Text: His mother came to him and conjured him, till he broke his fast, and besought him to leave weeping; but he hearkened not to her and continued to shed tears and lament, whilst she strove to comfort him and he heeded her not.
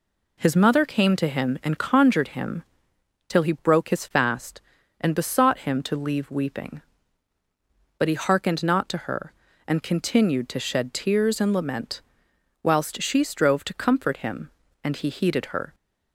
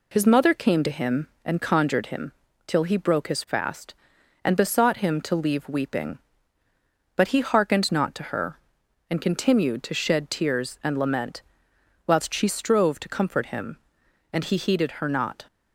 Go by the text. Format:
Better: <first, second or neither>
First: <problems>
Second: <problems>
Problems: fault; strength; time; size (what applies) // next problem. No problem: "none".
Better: second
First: stops before "not"; at 15.7 s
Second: none